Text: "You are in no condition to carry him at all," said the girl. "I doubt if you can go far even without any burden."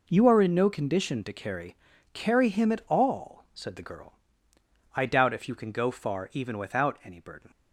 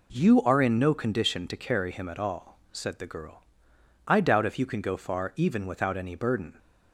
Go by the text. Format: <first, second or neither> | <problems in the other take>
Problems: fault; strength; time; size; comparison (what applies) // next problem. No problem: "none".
second | says "carry" twice; at 2.1 s